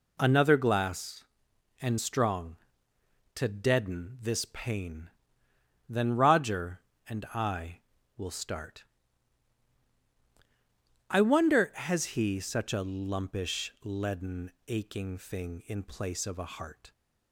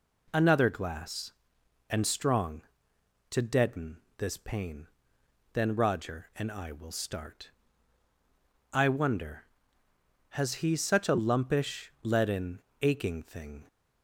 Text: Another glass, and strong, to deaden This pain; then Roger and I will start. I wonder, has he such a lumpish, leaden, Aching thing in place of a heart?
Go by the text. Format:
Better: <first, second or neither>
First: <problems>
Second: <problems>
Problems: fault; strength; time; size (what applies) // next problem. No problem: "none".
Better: first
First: none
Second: pauses between "deaden" and "This"; slight; at 3.9 s; 0.22 s long // stops before "in place of a heart"; at 13.6 s